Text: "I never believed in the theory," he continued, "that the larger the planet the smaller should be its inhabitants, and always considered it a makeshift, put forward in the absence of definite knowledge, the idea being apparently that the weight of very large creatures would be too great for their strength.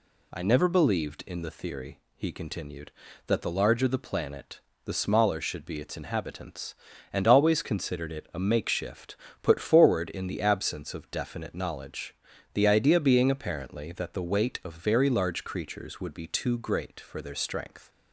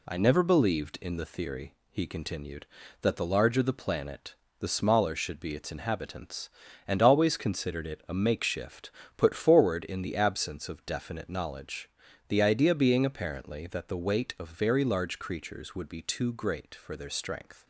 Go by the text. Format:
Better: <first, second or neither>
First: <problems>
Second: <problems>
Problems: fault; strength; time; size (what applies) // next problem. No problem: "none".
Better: first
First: pauses between "planet" and "the"; slight; at 4.6 s; 0.24 s long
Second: gets quieter; throughout; 4 dB // pauses between "planet" and "the"; slight; at 4.3 s; 0.24 s long